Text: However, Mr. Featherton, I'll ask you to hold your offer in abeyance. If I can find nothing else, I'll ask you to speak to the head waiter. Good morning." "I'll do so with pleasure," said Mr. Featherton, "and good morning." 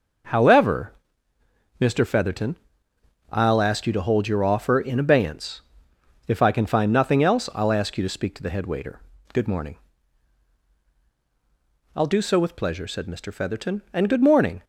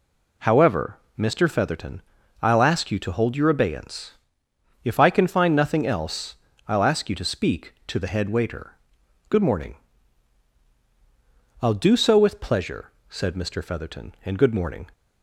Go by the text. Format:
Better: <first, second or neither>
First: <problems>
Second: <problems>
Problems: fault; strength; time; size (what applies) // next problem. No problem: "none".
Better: first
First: none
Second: skips "offer in"; at 3.4 s